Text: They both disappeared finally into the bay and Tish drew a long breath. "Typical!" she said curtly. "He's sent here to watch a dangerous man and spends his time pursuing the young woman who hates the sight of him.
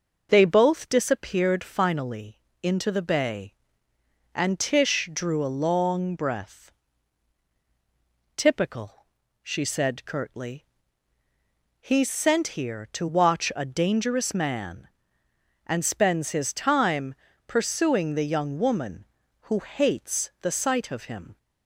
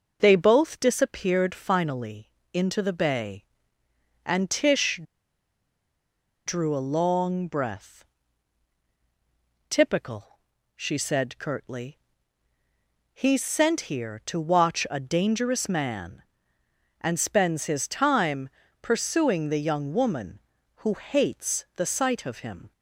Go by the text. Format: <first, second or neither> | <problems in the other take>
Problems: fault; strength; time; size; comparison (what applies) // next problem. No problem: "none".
first | pauses between "finally" and "into"; slight; at 2.2 s; 0.24 s long; slight in the first // pauses between "Tish" and "drew"; strong; at 5.0 s; 1.4 s long // pauses between "time" and "pursuing"; slight; at 18.4 s; 0.32 s long; slight in the first